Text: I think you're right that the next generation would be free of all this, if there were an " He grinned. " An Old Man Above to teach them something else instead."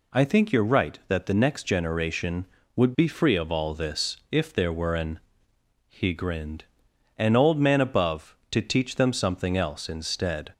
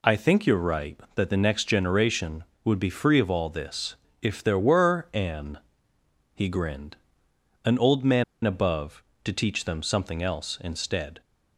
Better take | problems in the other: first | pauses between "Man" and "Above"; slight; at 8.2 s; 0.20 s long

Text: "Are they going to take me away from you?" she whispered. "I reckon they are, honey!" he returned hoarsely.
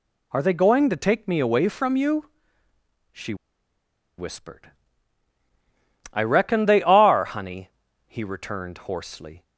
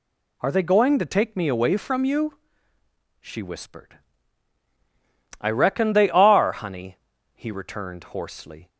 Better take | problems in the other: second | pauses between "she" and "whispered"; noticeable; at 3.3 s; 0.82 s long

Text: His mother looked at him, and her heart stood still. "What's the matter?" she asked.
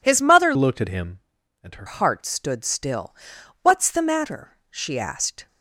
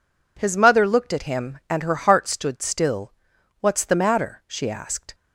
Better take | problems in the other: second | changes voice from "looked" to "her"; from 0.5 to 1.8 s; 1.3 s long

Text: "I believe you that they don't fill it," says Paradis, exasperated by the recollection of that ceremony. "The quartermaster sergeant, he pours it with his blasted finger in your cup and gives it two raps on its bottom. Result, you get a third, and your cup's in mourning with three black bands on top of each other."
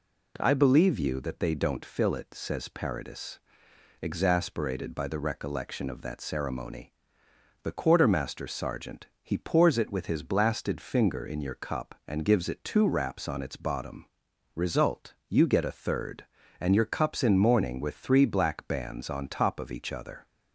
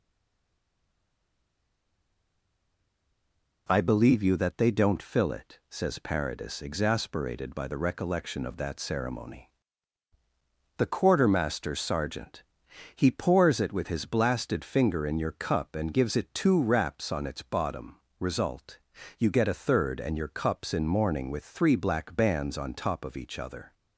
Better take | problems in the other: first | stays silent before the first word; strong; until 3.6 s; 3.6 s long

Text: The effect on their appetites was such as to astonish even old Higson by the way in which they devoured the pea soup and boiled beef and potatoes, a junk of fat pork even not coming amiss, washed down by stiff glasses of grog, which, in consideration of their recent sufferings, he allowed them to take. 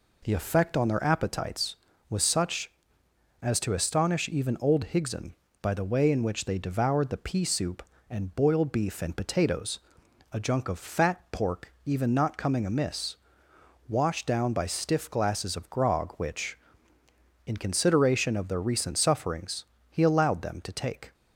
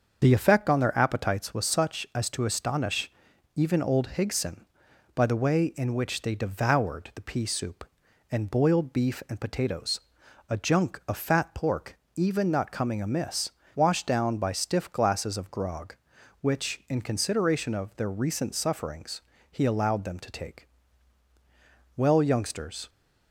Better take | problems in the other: first | starts louder than the rest; until 1.2 s; 6.5 dB // pauses between "astonish" and "even"; noticeable; at 3.1 s; 0.46 s long // pauses between "pork" and "even"; slight; at 11.9 s; 0.18 s long // goes on to say "Well youngsters"; noticeable; from 21.9 s on; 0.92 s long

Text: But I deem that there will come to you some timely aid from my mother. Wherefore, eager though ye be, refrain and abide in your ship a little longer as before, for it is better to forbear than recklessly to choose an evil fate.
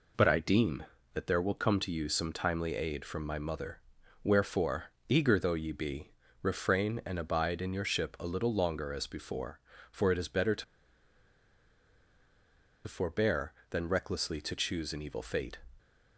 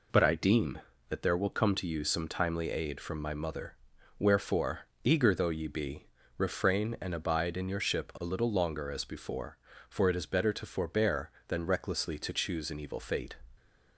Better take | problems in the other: second | pauses between "to" and "forbear"; strong; at 10.6 s; 2.2 s long

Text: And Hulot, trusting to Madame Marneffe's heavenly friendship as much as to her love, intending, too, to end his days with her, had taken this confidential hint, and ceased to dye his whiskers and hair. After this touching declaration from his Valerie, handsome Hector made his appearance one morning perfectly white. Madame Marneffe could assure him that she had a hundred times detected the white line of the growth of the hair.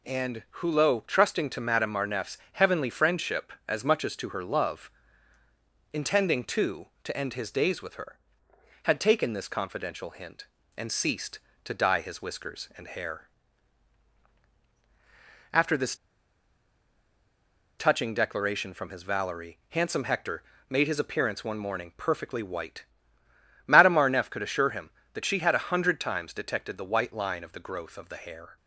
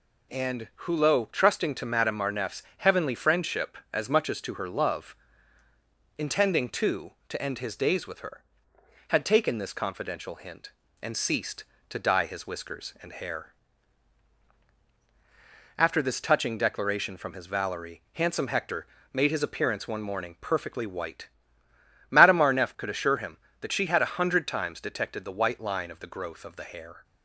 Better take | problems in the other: second | pauses between "And" and "Hulot"; slight; at 0.4 s; 0.18 s long; slight in the second // pauses between "Marneffe's" and "heavenly"; slight; at 2.3 s; 0.16 s long; slight in the second // pauses between "this" and "touching"; strong; at 15.9 s; 1.8 s long // pauses between "Hector" and "made"; slight; at 20.4 s; 0.26 s long; slight in the second

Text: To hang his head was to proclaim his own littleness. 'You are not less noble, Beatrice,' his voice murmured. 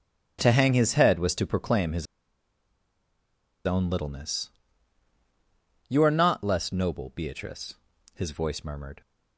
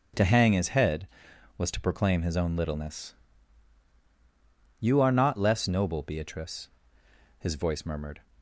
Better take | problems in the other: second | starts louder than the rest; strong; until 1.4 s; 10 dB; also in the second // pauses between "his" and "own"; strong; at 2.0 s; 1.6 s long

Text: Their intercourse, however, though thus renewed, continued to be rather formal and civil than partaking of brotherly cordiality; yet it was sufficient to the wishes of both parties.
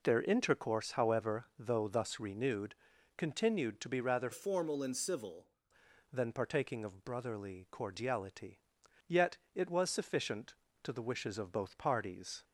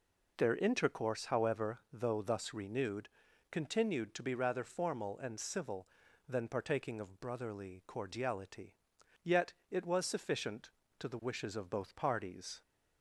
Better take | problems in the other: second | changes voice from "formal" to "civil"; from 4.3 to 5.5 s; 1.2 s long // pauses between "yet" and "it"; slight; at 9.3 s; 0.18 s long; slight in the second

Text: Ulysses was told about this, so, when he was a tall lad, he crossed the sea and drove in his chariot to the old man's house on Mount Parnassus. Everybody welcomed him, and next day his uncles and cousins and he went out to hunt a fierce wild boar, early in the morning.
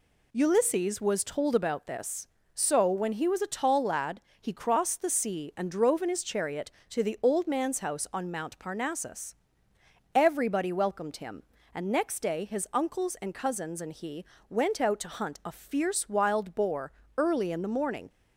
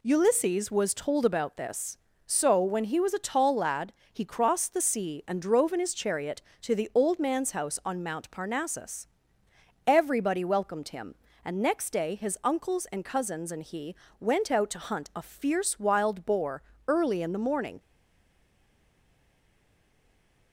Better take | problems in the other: first | pauses between "he" and "went"; slight; at 13.9 s; 0.24 s long; slight in the first // stays silent after the last word; strong; from 17.7 s on; 2.8 s long

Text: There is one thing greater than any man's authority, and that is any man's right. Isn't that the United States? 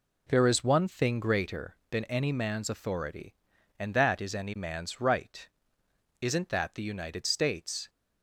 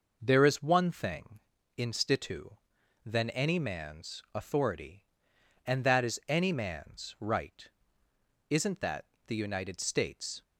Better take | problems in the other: first | says "institu" for "greater"; at 1.7 s // pauses between "that" and "the"; slight; at 9.0 s; 0.20 s long

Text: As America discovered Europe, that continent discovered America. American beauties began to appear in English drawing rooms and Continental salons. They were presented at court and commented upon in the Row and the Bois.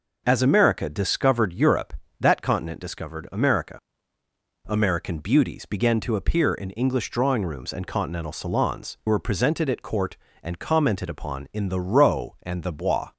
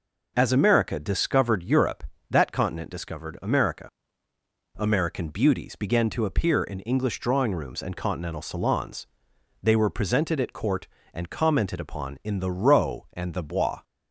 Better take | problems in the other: second | skips "They"; at 9.0 s

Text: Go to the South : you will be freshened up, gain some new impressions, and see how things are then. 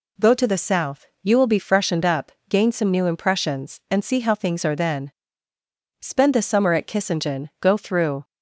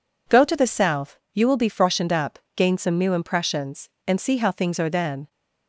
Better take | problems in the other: second | goes on to say "Spend the summer at Kissingen go through"; strong; from 5.9 s on; 2.2 s long

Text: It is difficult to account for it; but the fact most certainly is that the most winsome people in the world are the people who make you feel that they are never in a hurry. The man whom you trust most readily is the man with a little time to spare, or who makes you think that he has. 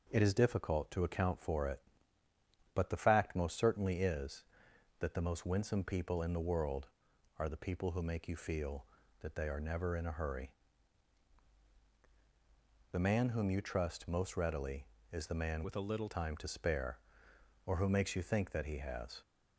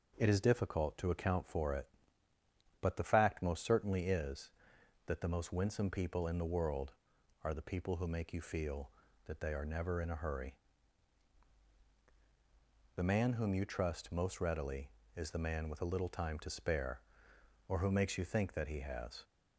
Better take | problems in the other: second | changes voice from "with" to "little"; from 15.6 to 16.0 s; 0.4 s long

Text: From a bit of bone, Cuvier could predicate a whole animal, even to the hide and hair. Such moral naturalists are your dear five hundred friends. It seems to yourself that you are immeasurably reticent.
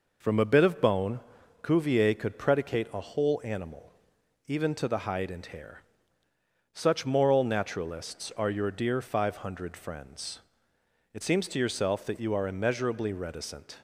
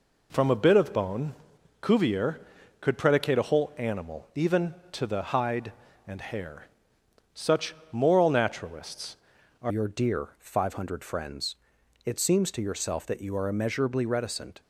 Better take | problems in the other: first | pauses between "Such" and "moral"; slight; at 7.7 s; 0.16 s long // changes voice at "your"; from 9.6 s on; 4.9 s long

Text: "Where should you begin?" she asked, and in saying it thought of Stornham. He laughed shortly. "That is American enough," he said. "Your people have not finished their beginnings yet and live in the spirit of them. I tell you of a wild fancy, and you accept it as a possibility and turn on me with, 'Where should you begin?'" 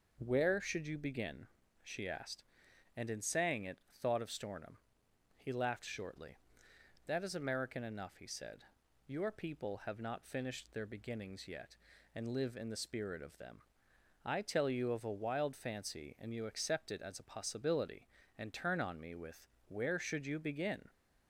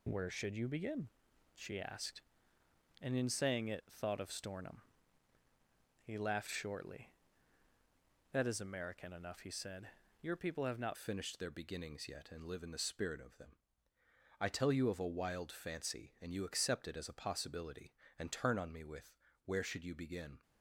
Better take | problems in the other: first | changes voice at "finished"; from 10.9 s on; 9.5 s long

